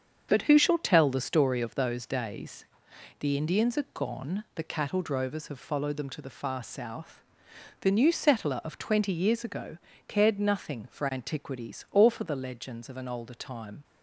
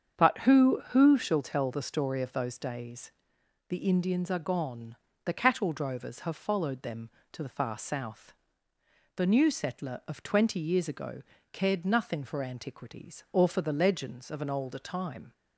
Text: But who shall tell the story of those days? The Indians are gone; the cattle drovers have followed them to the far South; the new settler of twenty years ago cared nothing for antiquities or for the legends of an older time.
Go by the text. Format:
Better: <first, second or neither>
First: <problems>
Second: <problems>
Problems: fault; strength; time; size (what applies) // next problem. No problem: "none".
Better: first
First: starts louder than the rest; strong; until 1.3 s; 7 dB // pauses between "ago" and "cared"; slight; at 9.7 s; 0.28 s long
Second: starts louder than the rest; strong; until 1.2 s; 7.5 dB // says "who" twice; at 0.8 s // pauses between "ago" and "cared"; slight; at 11.2 s; 0.28 s long